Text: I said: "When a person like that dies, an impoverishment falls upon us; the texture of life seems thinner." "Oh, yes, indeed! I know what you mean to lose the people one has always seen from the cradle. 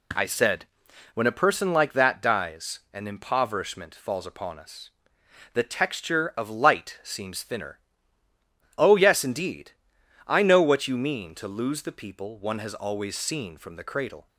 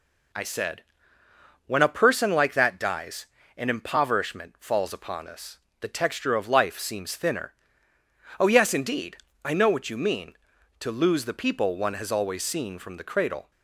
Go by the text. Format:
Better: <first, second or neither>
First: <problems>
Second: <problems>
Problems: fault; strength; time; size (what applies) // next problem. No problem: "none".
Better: second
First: says "light" for "life"; at 6.4 s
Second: none